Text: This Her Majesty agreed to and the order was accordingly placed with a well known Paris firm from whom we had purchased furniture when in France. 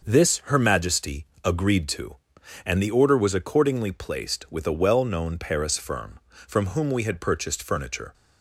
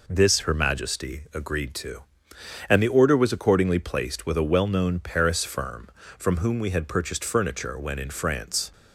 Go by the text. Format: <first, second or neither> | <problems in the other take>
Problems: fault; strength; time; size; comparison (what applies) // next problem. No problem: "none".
second | starts louder than the rest; until 1.0 s; 6.5 dB // pauses between "Majesty" and "agreed"; slight; at 1.2 s; 0.18 s long // stops before "when in France"; at 8.1 s